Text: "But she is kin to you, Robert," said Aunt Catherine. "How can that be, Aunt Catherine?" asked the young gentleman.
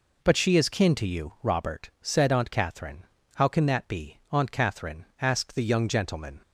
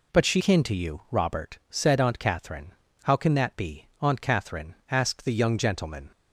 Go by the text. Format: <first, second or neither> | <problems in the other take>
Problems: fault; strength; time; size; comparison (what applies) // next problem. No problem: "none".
first | skips "is"; at 0.4 s